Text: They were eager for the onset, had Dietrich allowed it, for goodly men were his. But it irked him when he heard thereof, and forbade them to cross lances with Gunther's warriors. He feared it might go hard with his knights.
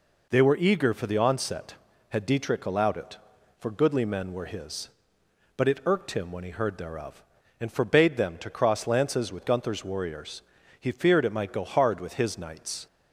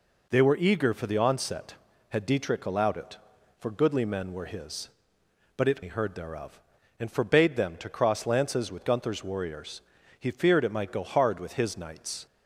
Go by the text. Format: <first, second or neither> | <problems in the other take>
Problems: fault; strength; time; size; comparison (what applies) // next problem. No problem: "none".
first | skips "irked him when"; at 5.8 s